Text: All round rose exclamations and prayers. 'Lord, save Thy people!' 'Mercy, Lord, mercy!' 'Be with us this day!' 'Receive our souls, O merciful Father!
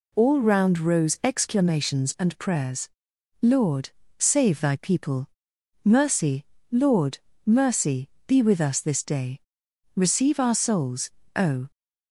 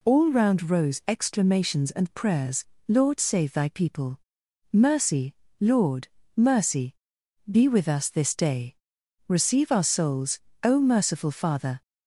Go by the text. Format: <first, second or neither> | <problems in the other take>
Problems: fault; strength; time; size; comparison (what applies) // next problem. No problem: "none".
second | stops before "merciful Father"; at 11.7 s